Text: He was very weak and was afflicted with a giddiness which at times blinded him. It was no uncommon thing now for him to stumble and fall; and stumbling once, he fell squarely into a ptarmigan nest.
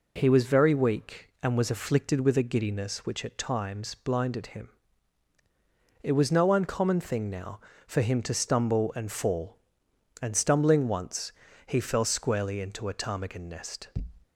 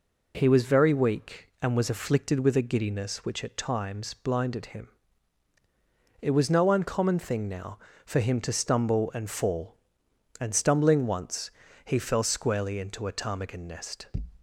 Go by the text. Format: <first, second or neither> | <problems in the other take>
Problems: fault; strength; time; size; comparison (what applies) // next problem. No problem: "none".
neither | none